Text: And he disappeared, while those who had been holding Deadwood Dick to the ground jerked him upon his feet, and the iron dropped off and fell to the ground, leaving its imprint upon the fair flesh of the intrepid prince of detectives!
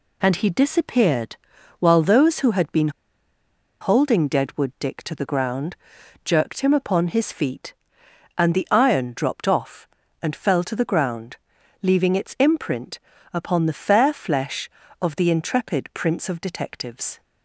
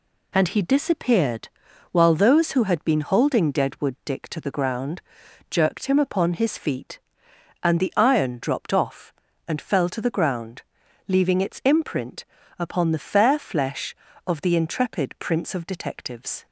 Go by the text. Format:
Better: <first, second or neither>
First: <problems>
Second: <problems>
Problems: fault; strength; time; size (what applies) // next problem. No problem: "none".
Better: second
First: pauses between "been" and "holding"; noticeable; at 2.8 s; 0.91 s long // pauses between "ground" and "jerked"; noticeable; at 5.7 s; 0.50 s long // pauses between "imprint" and "upon"; slight; at 12.9 s; 0.34 s long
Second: pauses between "ground" and "jerked"; noticeable; at 4.9 s; 0.50 s long // pauses between "imprint" and "upon"; slight; at 12.2 s; 0.34 s long